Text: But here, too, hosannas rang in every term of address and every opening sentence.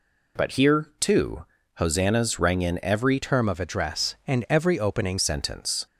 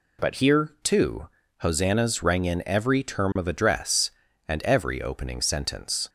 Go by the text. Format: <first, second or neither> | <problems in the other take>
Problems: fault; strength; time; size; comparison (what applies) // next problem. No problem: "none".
second | changes voice from "term" to "opening"; from 3.2 to 5.1 s; 1.9 s long